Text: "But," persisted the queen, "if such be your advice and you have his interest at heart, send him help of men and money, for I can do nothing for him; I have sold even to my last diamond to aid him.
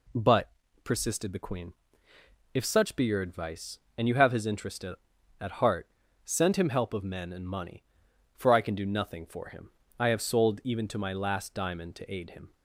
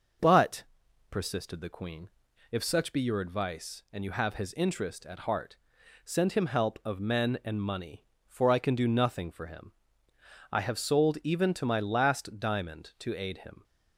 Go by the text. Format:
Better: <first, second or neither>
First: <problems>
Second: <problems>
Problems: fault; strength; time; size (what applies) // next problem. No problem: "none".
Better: second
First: says "at" twice; at 5.3 s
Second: none